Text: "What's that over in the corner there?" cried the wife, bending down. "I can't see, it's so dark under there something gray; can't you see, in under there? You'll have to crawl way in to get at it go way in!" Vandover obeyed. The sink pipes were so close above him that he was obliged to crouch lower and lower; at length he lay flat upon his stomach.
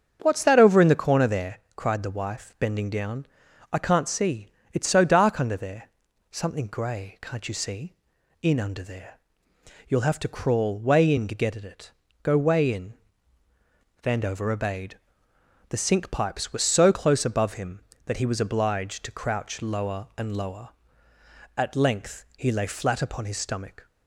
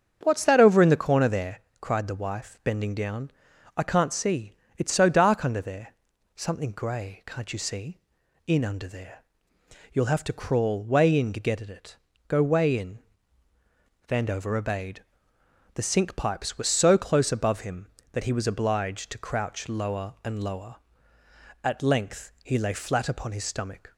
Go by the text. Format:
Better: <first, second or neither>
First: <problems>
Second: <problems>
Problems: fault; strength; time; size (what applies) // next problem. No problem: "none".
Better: neither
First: starts louder than the rest; strong; until 1.2 s; 7.5 dB // pauses between "there" and "something"; at 5.8 s; 0.42 s long // pauses between "it" and "go"; slight; at 11.9 s; 0.30 s long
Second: starts louder than the rest; strong; until 1.2 s; 7.5 dB // pauses between "there" and "something"; at 5.9 s; 0.42 s long // pauses between "it" and "go"; slight; at 11.9 s; 0.30 s long